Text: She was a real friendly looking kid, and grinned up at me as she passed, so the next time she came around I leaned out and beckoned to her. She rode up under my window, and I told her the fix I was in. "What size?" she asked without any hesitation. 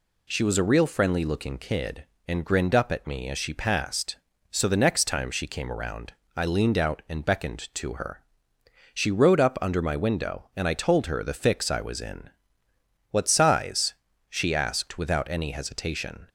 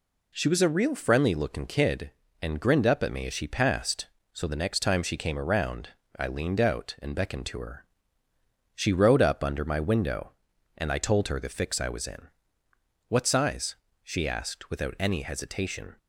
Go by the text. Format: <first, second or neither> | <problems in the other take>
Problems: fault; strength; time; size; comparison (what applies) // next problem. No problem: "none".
neither | pauses between "around" and "I"; slight; the same in both